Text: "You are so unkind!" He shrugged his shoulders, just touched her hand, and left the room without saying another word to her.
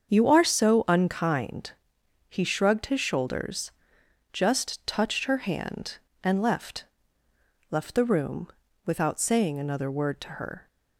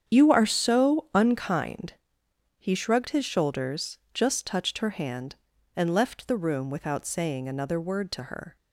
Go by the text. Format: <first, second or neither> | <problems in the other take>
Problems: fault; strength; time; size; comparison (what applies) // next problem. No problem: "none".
second | starts louder than the rest; until 1.1 s; 7 dB; strong in the second // says "left" twice; at 7.6 s // pauses between "room" and "without"; at 8.4 s; 0.40 s long